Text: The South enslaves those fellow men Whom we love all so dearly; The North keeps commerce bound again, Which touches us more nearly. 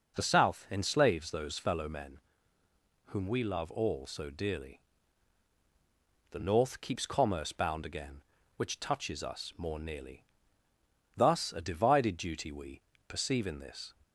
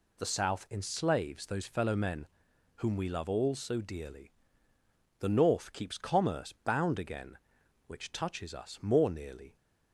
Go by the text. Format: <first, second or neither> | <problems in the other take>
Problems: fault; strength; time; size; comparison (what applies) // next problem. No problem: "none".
second | pauses between "men" and "Whom"; noticeable; at 2.1 s; 0.88 s long; noticeable in the second // goes on to say "Thus a divided duty we Perceive in this"; strong; from 11.1 s on; 2.7 s long